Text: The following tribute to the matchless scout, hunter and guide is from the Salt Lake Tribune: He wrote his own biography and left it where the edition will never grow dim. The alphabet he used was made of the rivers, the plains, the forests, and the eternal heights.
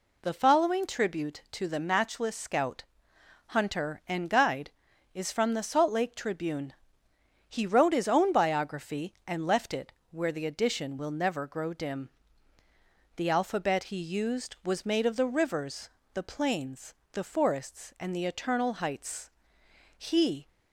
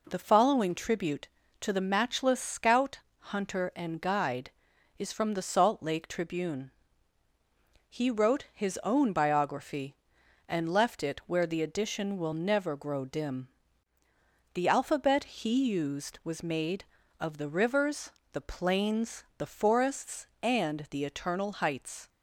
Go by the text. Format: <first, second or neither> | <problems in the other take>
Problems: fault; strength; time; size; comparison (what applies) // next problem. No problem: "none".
second | pauses between "it" and "where"; slight; at 9.9 s; 0.18 s long // goes on to say "He"; from 19.9 s on; 0.52 s long